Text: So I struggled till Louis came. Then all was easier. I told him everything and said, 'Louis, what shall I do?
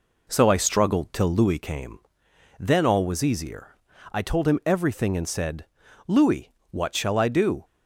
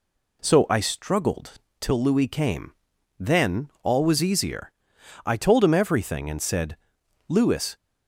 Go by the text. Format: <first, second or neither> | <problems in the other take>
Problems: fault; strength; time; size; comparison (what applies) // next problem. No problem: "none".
first | pauses between "struggled" and "till"; slight; at 1.5 s; 0.26 s long // stops before "what shall I do"; at 7.7 s